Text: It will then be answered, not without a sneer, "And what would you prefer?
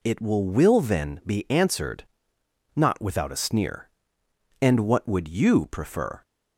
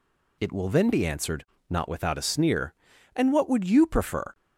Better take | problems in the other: second | says "will" twice; at 0.4 s

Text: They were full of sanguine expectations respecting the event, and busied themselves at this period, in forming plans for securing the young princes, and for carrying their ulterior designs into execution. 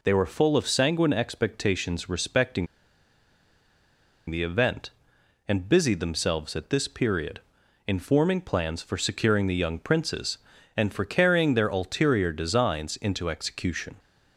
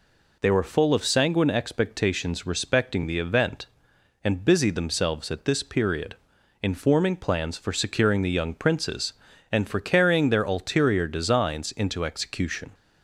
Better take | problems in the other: second | pauses between "respecting" and "the"; strong; at 2.6 s; 1.6 s long

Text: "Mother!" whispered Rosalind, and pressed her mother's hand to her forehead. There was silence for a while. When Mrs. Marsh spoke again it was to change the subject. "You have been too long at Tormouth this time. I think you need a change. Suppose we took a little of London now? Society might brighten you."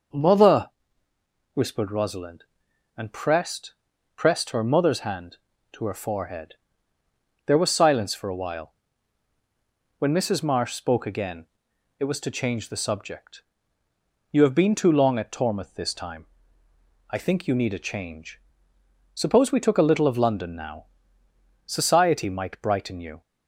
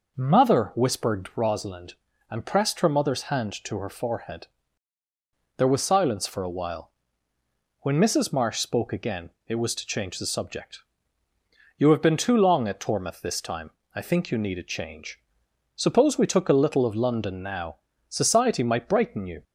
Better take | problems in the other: second | says "pressed" twice; at 4.1 s // pauses between "again" and "it"; noticeable; at 11.4 s; 0.52 s long; slight in the second

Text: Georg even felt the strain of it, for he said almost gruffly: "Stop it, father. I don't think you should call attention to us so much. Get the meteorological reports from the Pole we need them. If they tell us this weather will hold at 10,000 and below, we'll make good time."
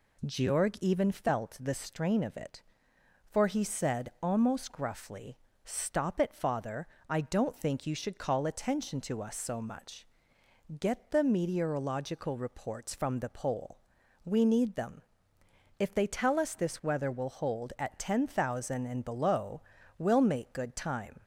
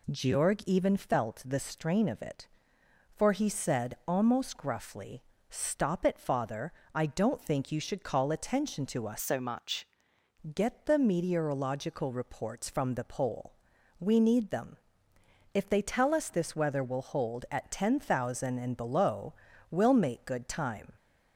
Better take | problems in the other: first | changes voice from "so" to "much"; from 9.1 to 9.8 s; 0.7 s long // pauses between "Pole" and "we"; noticeable; at 13.5 s; 0.48 s long; noticeable in the first

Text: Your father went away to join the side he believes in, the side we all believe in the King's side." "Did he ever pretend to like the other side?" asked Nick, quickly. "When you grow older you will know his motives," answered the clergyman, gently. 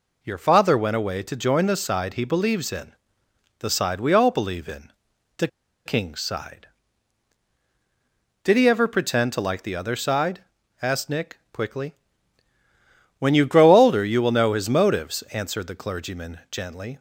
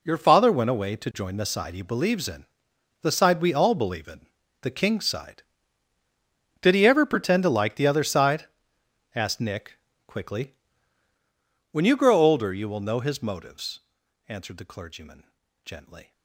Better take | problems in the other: second | pauses between "in" and "the"; noticeable; at 4.9 s; 0.46 s long; slight in the second // pauses between "the" and "King's"; at 5.4 s; 0.38 s long

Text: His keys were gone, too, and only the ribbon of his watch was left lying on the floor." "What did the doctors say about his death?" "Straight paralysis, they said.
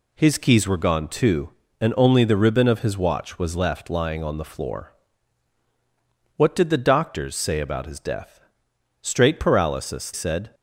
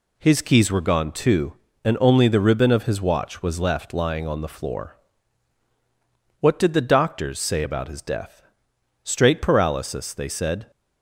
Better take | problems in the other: second | skips "they"; at 10.1 s

